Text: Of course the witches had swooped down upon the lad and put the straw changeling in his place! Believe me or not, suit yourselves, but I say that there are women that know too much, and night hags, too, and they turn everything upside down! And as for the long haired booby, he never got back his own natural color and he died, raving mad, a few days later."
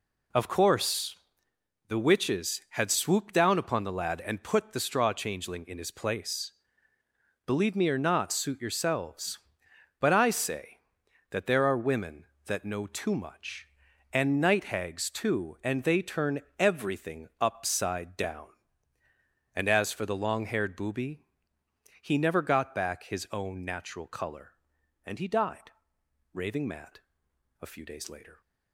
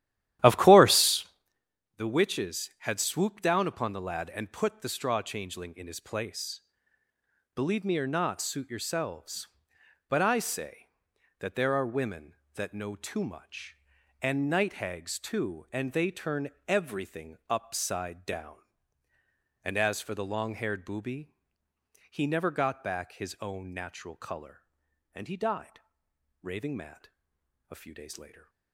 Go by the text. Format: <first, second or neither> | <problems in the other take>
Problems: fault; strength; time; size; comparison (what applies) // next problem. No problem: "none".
first | starts louder than the rest; strong; until 1.5 s; 13 dB // pauses between "course" and "the"; noticeable; at 1.2 s; 0.72 s long; noticeable in the first // pauses between "turn" and "everything"; slight; at 16.5 s; 0.18 s long; slight in the first